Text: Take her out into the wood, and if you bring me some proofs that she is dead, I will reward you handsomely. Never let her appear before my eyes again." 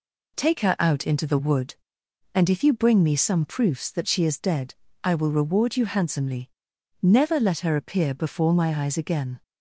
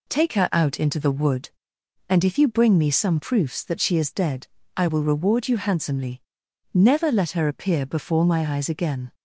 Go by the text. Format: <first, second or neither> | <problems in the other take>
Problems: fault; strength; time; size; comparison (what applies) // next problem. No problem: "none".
neither | none